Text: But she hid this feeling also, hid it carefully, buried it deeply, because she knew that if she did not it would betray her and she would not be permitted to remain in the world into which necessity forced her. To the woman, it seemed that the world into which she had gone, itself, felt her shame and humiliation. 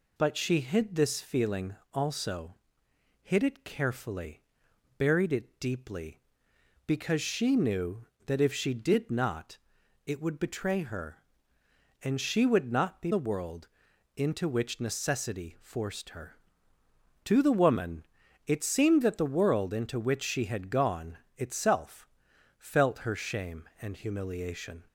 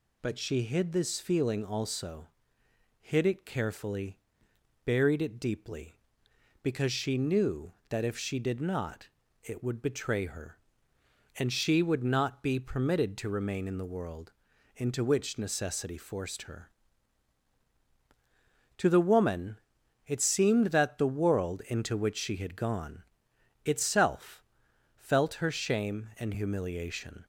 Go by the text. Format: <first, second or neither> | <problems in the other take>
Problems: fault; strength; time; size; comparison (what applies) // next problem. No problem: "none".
second | pauses between "feeling" and "also"; slight; at 1.7 s; 0.18 s long // pauses between "not" and "it"; noticeable; at 9.5 s; 0.48 s long; slight in the second // skips "permitted to remain in"; at 13.1 s // pauses between "world" and "into"; noticeable; at 13.6 s; 0.48 s long; also in the second